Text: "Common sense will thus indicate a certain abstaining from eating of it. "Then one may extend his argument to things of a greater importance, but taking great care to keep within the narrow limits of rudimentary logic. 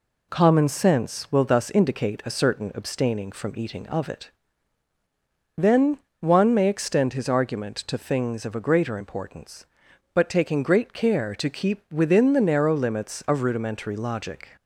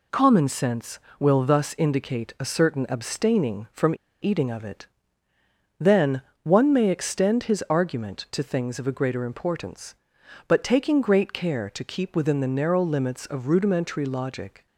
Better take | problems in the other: first | pauses between "from" and "eating"; slight; at 3.9 s; 0.28 s long // pauses between "Then" and "one"; slight; at 6.2 s; 0.20 s long; slight in the first

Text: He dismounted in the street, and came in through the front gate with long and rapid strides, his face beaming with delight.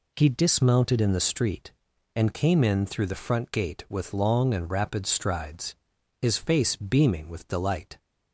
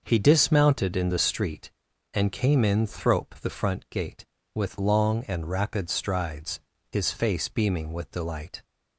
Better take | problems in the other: first | says "thrope" for "through"; at 2.8 s

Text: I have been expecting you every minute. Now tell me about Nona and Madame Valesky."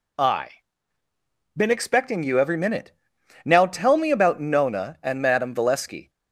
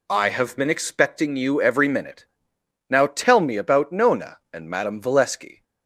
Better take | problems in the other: second | skips "have"; at 1.0 s

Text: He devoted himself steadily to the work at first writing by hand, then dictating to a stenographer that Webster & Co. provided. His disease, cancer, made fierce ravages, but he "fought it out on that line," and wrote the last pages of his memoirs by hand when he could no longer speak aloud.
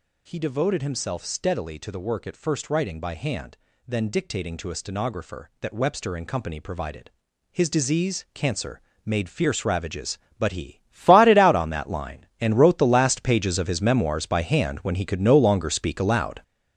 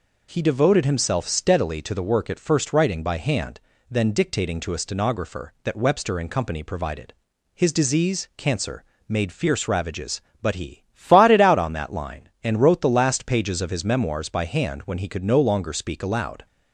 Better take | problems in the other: second | gets louder; strong; throughout; 8 dB

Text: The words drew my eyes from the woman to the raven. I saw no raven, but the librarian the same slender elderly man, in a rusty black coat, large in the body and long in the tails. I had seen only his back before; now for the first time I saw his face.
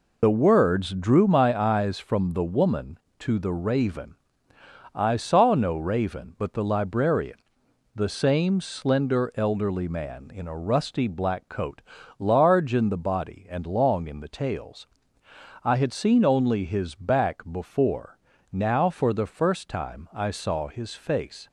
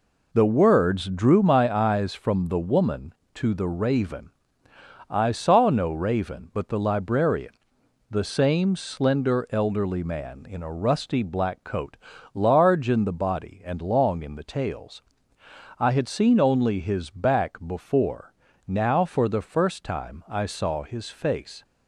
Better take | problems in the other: second | loses the start of "The"; at 0.2 s; 45 ms // pauses between "librarian" and "the"; noticeable; at 7.3 s; 0.56 s long; noticeable in the second

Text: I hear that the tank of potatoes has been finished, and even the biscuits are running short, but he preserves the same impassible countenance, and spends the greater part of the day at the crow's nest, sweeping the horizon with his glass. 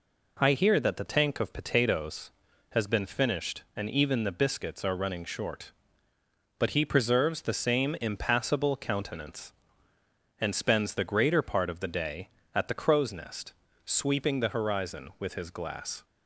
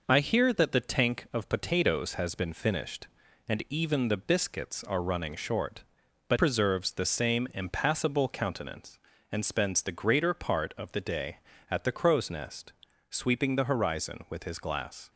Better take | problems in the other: first | skips "he"; at 6.3 s

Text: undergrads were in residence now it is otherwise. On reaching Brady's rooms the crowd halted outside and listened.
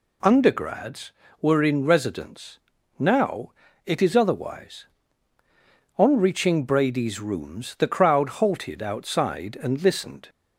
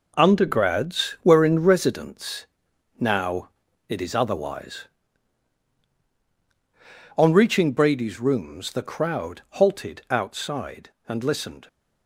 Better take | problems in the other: first | gets quieter; strong; throughout; 9 dB // pauses between "residence" and "now"; noticeable; at 2.4 s; 0.54 s long; also in the first // pauses between "now" and "it"; at 3.4 s; 0.40 s long; slight in the first

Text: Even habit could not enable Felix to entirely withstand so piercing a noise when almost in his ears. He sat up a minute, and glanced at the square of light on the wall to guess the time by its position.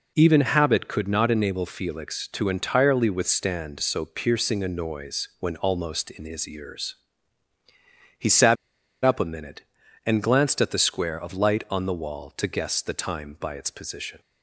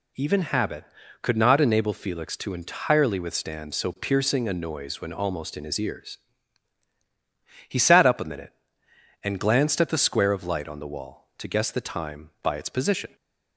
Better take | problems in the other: second | pauses between "sat" and "up"; noticeable; at 8.5 s; 0.48 s long

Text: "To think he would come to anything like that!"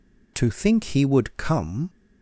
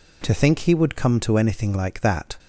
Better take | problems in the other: second | stops before "to anything like that"; at 1.8 s

